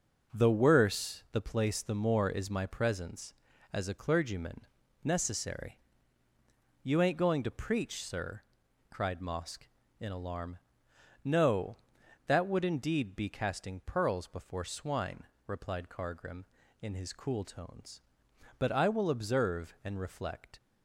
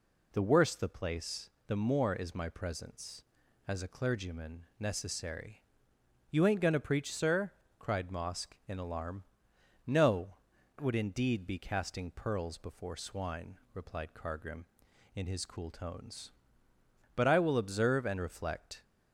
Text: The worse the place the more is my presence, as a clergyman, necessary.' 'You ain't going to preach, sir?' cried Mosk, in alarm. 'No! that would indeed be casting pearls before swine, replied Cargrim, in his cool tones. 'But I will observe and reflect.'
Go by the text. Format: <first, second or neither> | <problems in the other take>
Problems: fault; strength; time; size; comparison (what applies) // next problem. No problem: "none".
first | pauses between "place" and "the"; slight; at 1.4 s; 0.18 s long // skips "that"; at 10.5 s